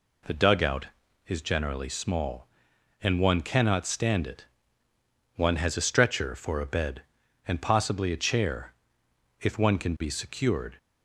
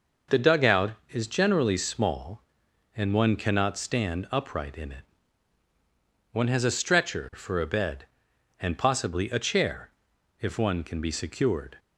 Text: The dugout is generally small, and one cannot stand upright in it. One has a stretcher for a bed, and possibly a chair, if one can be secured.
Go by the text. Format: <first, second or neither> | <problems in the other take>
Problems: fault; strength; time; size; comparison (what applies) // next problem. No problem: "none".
second | skips "upright in"; at 4.2 s